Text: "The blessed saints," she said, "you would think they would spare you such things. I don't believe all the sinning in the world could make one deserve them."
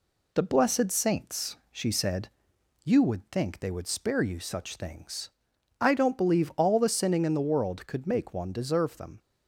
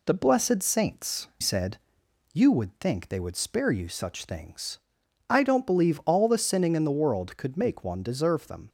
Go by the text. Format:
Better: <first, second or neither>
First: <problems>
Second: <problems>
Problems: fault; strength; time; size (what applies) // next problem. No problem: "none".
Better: first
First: none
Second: skips "she"; at 1.3 s